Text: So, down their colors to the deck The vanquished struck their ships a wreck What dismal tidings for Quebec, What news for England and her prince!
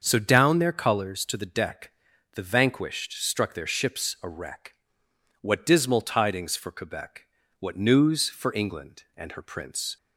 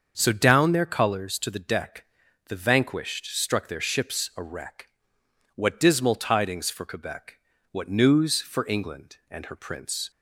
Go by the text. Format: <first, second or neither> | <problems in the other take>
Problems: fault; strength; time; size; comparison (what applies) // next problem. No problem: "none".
neither | starts louder than the rest; the same in both // pauses between "deck" and "The"; the same in both // pauses between "wreck" and "What"; noticeable; the same in both